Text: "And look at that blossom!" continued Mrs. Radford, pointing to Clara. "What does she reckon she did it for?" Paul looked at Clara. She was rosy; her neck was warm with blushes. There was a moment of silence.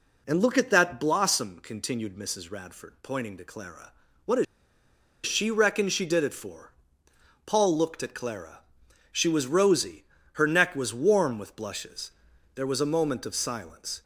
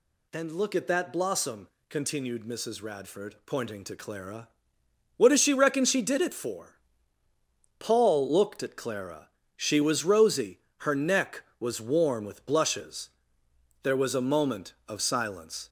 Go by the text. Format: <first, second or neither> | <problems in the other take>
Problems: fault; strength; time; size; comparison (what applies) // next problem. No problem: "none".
second | pauses between "does" and "she"; noticeable; at 4.4 s; 0.81 s long